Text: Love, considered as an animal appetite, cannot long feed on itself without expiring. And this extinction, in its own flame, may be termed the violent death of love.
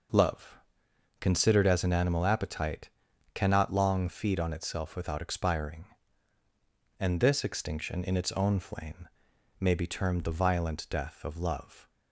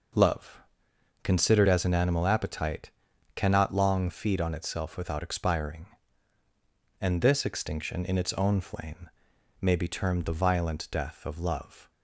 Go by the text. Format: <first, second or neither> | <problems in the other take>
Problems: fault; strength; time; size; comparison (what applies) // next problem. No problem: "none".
neither | none